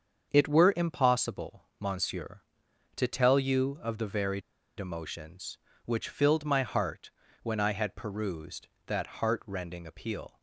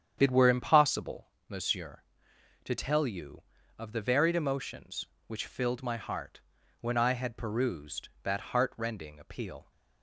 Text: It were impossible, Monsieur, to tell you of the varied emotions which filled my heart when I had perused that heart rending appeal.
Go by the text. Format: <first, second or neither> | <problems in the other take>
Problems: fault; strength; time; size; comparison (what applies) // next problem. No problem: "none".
second | starts louder than the rest; until 1.3 s; 7 dB; strong in the second // pauses between "varied" and "emotions"; at 4.4 s; 0.38 s long // pauses between "heart" and "when"; slight; at 7.1 s; 0.32 s long; also in the second